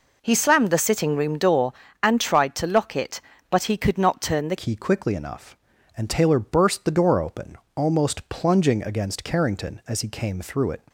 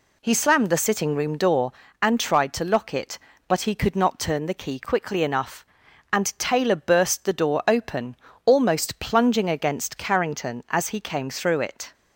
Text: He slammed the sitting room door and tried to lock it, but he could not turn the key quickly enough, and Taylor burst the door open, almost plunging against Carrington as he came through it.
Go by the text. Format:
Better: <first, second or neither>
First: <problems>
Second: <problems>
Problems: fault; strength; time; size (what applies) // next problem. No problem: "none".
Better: second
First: changes voice at "key"; from 4.5 s on; 6.3 s long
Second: none